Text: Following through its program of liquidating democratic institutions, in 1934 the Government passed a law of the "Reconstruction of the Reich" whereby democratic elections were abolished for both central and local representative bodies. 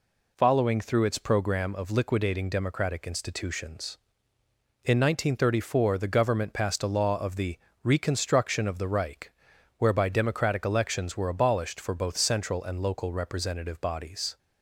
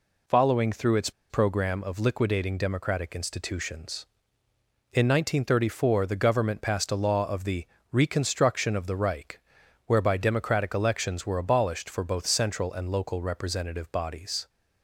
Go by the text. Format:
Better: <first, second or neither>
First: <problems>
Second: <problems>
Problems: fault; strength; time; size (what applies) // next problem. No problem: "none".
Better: first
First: pauses between "the" and "Reconstruction"; slight; at 7.5 s; 0.28 s long // pauses between "Reich" and "whereby"; noticeable; at 9.3 s; 0.48 s long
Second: pauses between "its" and "program"; slight; at 1.0 s; 0.19 s long // pauses between "the" and "Reconstruction"; slight; at 7.6 s; 0.28 s long // pauses between "Reich" and "whereby"; noticeable; at 9.3 s; 0.48 s long